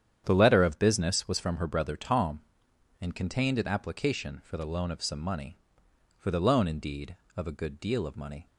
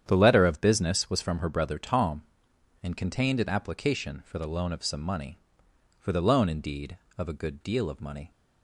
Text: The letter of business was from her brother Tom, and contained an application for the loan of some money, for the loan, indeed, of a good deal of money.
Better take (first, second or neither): neither